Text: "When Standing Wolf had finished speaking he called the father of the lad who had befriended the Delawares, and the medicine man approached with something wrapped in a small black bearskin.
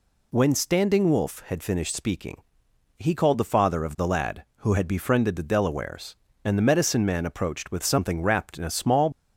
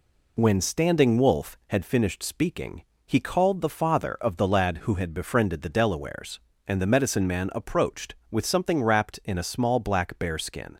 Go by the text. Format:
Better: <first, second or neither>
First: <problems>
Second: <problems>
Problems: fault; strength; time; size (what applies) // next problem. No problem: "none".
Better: second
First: pauses between "speaking" and "he"; noticeable; at 2.4 s; 0.56 s long // stops before "black bearskin"; at 9.1 s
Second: pauses between "speaking" and "he"; slight; at 2.8 s; 0.20 s long